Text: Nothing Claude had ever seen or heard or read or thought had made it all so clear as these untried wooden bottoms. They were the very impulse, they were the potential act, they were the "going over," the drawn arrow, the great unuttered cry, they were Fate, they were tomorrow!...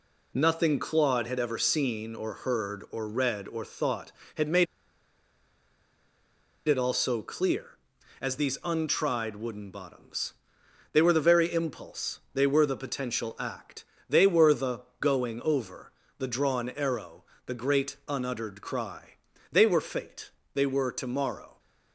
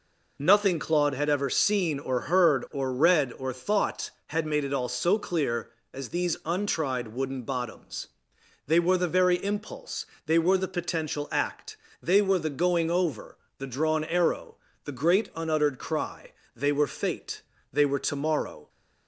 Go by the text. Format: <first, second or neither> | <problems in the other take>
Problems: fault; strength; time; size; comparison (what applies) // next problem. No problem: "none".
second | pauses between "made" and "it"; strong; at 4.6 s; 2.0 s long // pauses between "the" and "going"; slight; at 14.8 s; 0.18 s long